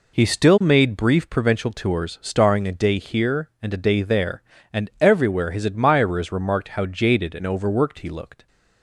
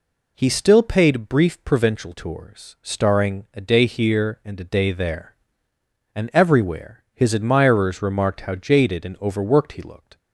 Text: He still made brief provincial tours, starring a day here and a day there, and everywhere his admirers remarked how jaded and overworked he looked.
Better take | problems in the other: first | says "paid" for "made"; at 0.8 s

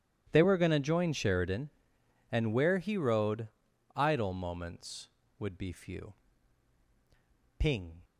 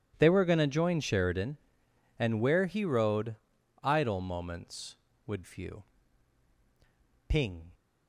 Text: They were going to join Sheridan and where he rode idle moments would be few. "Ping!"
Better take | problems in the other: first | pauses between "rode" and "idle"; noticeable; at 3.3 s; 0.48 s long; noticeable in the first // skips "be"; at 5.4 s

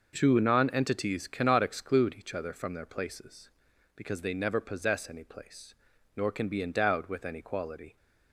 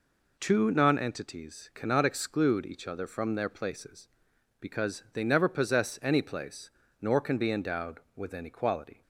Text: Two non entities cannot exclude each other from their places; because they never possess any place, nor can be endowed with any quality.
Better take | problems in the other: neither | none

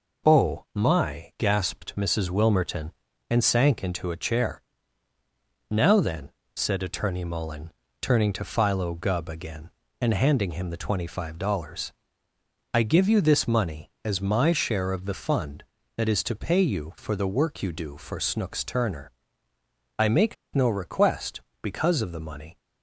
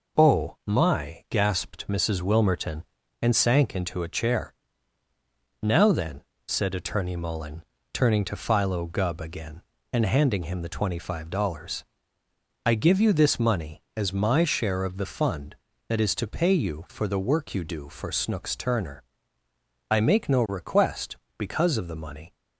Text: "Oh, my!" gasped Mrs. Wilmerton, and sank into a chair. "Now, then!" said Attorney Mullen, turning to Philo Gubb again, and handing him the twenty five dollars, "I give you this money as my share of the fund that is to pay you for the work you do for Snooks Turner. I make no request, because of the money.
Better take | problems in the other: second | pauses between "make" and "no"; slight; at 20.3 s; 0.20 s long

